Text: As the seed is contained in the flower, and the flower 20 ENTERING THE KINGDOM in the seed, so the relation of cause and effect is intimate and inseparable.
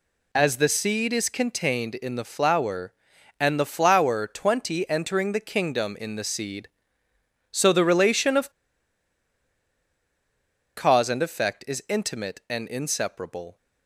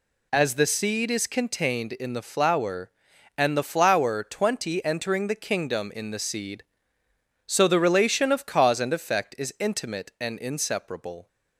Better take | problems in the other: second | pauses between "of" and "cause"; strong; at 8.4 s; 2.2 s long

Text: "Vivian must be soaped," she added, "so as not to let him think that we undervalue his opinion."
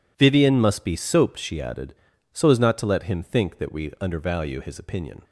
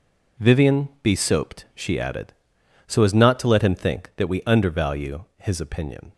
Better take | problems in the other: first | skips "must"; at 0.9 s

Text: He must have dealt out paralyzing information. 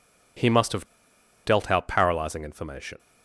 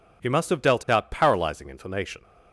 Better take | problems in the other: second | pauses between "have" and "dealt"; noticeable; at 0.8 s; 0.59 s long

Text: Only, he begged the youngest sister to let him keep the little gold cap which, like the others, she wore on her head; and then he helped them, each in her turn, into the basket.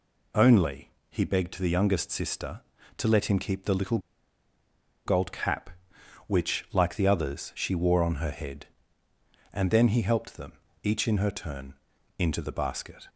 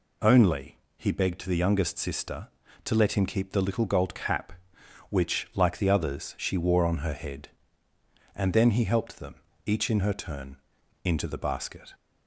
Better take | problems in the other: second | pauses between "little" and "gold"; at 3.9 s; 1.0 s long

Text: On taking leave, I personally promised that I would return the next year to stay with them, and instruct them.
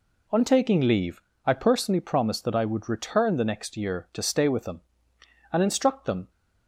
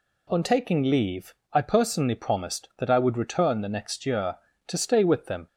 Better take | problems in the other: first | stops before "and instruct them"; at 5.4 s

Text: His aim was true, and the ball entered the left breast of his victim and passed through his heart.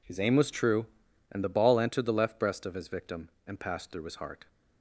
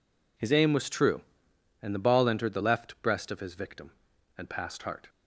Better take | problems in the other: first | skips "through his"; at 4.8 s

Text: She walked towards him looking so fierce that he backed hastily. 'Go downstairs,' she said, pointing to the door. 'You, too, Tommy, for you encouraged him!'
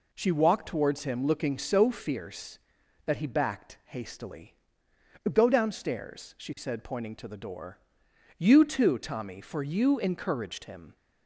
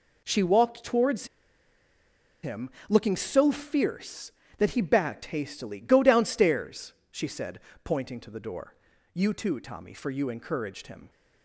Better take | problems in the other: first | pauses between "towards" and "him"; at 1.2 s; 1.1 s long // pauses between "him" and "looking"; slight; at 2.6 s; 0.18 s long

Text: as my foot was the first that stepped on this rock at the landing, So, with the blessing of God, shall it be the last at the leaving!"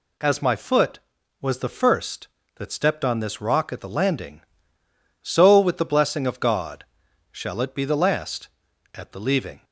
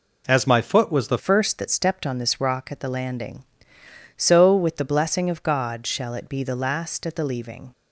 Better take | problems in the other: first | changes voice at "first"; from 1.1 s on; 6.6 s long

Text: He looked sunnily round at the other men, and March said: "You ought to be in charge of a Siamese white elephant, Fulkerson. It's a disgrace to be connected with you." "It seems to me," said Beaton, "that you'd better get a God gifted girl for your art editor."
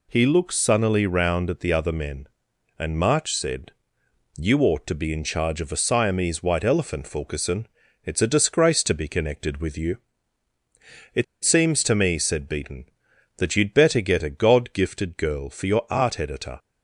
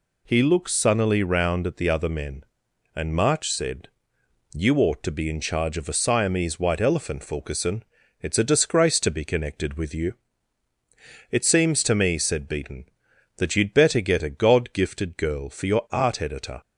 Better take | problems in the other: second | pauses between "It" and "seems"; slight; at 11.2 s; 0.19 s long

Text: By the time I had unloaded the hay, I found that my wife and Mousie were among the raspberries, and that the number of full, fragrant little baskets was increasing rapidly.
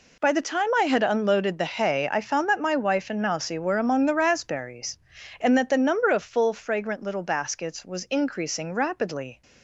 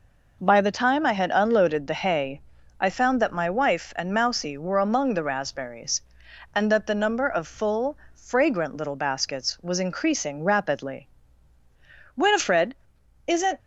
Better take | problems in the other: first | goes on to say "Winifred isn't"; from 12.1 s on; 1.4 s long

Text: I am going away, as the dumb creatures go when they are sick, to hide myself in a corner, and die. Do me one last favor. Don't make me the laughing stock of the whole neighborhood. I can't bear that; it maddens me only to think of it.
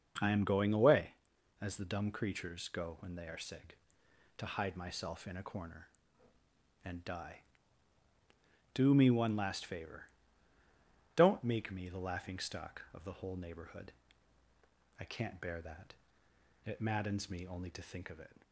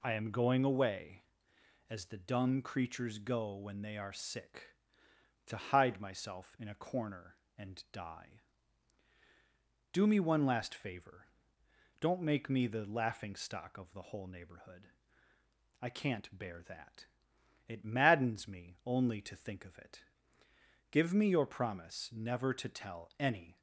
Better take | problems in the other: first | goes on to say "Give me your promise never to tell any"; strong; from 20.9 s on; 2.6 s long

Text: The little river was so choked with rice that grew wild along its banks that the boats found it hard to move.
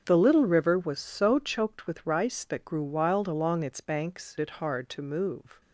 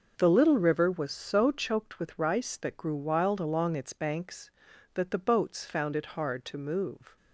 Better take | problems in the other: second | starts louder than the rest; until 1.0 s; 7 dB // skips "that the boats found"; at 4.3 s

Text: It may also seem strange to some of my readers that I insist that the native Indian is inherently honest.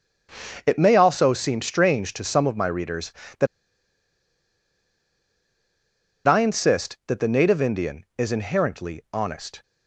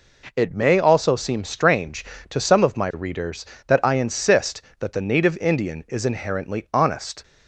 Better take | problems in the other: second | starts louder than the rest; strong; until 1.6 s; 7.5 dB // pauses between "that" and "I"; strong; at 3.4 s; 2.8 s long

